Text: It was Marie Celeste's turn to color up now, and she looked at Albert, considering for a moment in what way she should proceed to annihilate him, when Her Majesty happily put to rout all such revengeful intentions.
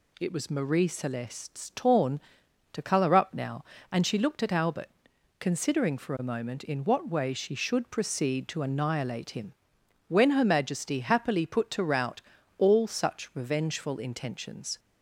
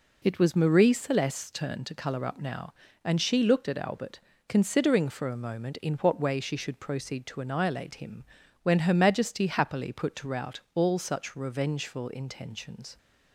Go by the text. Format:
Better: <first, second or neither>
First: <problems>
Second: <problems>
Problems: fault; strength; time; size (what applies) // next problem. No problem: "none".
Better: second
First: says "torn" for "turn"; at 1.7 s // pauses between "rout" and "all"; slight; at 12.2 s; 0.36 s long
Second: pauses between "rout" and "all"; slight; at 10.5 s; 0.16 s long